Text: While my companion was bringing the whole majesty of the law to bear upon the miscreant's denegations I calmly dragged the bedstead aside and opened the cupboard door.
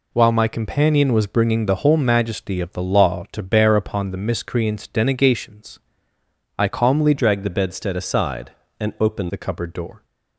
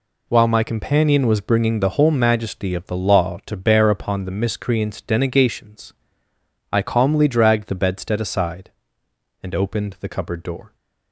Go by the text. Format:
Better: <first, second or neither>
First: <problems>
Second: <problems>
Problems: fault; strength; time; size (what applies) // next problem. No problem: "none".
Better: second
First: pauses between "denegations" and "I"; noticeable; at 5.7 s; 0.80 s long // changes voice from "dragged" to "opened"; from 7.1 to 9.3 s; 2.2 s long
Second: pauses between "denegations" and "I"; noticeable; at 5.9 s; 0.80 s long